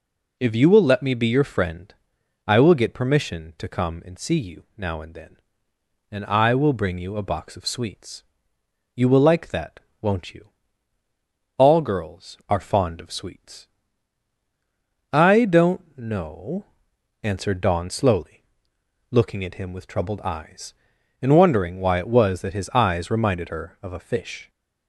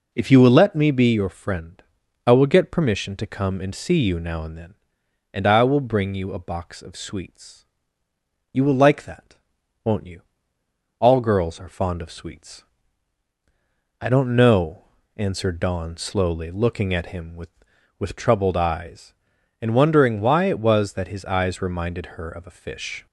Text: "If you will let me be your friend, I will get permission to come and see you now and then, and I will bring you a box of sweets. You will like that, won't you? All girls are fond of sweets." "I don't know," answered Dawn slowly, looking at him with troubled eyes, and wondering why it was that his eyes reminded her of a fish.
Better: first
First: none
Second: says "with" twice; at 17.9 s

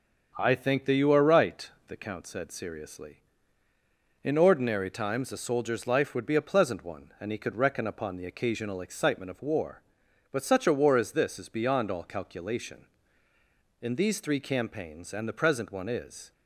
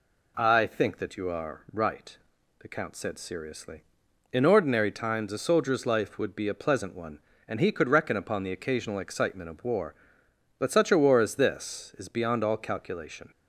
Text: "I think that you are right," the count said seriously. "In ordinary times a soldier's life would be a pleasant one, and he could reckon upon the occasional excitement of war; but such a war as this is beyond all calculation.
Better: second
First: starts louder than the rest; until 1.3 s; 6.5 dB // goes on to say "In these three campaigns and the present one is"; strong; from 13.7 s on; 2.5 s long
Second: none

